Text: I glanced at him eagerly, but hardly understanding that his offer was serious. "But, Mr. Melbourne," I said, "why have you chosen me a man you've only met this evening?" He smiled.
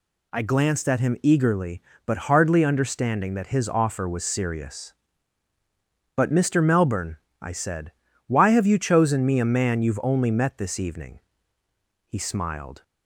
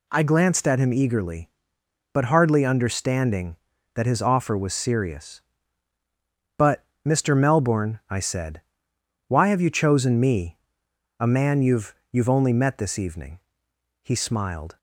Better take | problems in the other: first | pauses between "me" and "a"; noticeable; at 10.5 s; 0.62 s long // says "you've" twice; at 12.0 s

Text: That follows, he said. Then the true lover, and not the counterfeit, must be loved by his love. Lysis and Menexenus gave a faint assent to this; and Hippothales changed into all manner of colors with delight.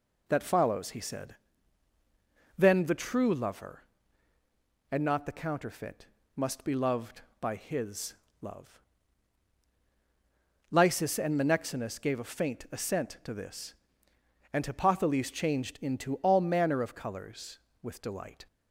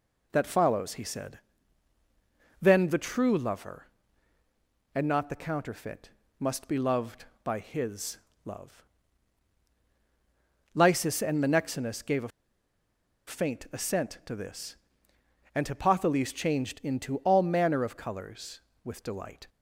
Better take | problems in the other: first | pauses between "his" and "love"; slight; at 8.1 s; 0.26 s long; slight in the first // pauses between "a" and "faint"; at 12.2 s; 0.99 s long

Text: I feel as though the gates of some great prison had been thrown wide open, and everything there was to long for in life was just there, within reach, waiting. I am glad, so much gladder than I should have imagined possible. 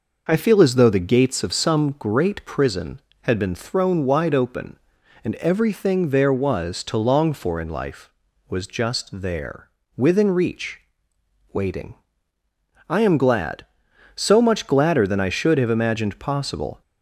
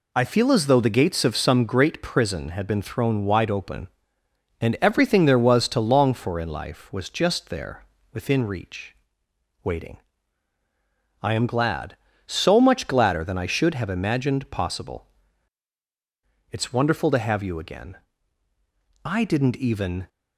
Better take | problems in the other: first | goes on to say "It's wonderful to have you again I didn't even"; strong; from 16.4 s on; 3.5 s long

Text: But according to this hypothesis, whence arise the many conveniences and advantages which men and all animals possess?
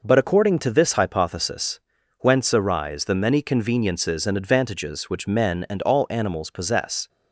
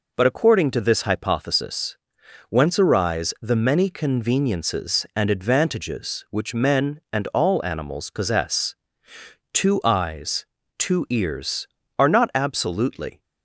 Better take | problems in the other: first | goes on to say "Two eyes two ears are not absolutely"; strong; from 9.5 s on; 3.6 s long

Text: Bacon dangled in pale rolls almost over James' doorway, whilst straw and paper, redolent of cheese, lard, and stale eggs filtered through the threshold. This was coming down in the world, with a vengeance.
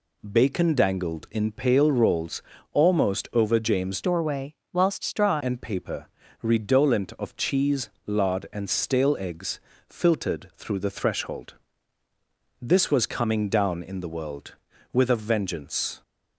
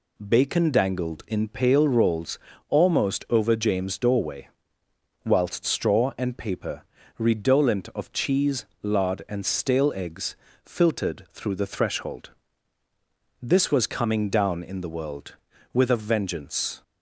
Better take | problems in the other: second | pauses between "rolls" and "almost"; slight; at 2.4 s; 0.32 s long; slight in the second // changes voice from "doorway" to "straw"; from 4.0 to 5.4 s; 1.4 s long // pauses between "eggs" and "filtered"; slight; at 9.5 s; 0.30 s long; slight in the second

